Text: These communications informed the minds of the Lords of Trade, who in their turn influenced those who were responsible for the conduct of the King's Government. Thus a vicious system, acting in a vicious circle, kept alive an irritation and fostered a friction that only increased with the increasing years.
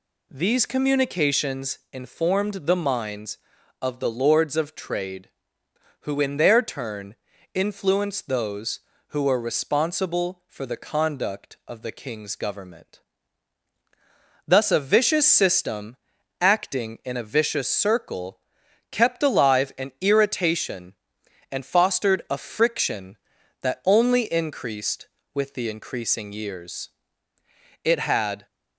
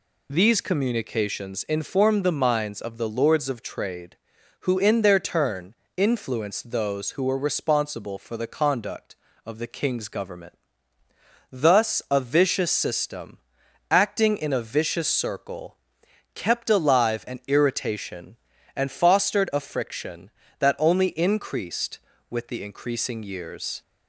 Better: second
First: pauses between "turn" and "influenced"; slight; at 7.1 s; 0.36 s long // goes on to say "It had"; noticeable; from 27.8 s on; 0.62 s long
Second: pauses between "turn" and "influenced"; slight; at 5.7 s; 0.24 s long

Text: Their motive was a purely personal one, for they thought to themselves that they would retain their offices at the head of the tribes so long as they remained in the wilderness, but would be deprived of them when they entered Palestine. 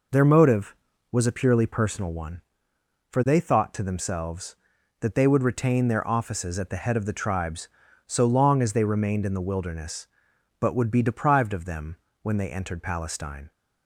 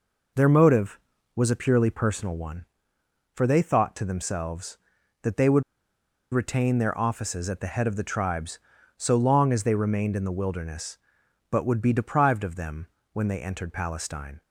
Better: first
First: pauses between "them" and "when"; slight; at 11.9 s; 0.28 s long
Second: pauses between "would" and "retain"; noticeable; at 5.6 s; 0.70 s long // pauses between "them" and "when"; slight; at 12.8 s; 0.28 s long

